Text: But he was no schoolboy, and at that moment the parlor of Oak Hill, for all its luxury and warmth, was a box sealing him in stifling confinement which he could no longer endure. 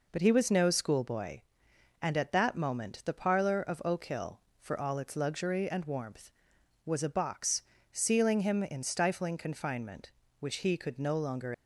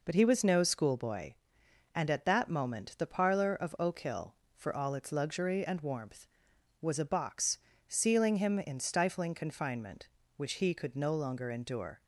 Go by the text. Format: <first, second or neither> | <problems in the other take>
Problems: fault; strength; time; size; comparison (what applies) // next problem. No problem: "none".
second | pauses between "box" and "sealing"; slight; at 7.6 s; 0.30 s long; slight in the second // stops before "endure"; at 11.5 s